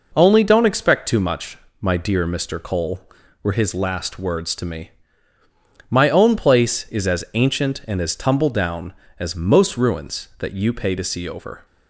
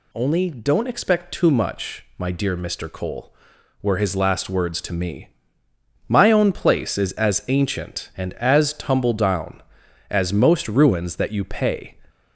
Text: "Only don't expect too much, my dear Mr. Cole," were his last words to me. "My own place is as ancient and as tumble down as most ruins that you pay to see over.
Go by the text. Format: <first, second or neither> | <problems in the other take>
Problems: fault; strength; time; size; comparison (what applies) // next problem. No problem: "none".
first | stops before "to see over"; at 12.0 s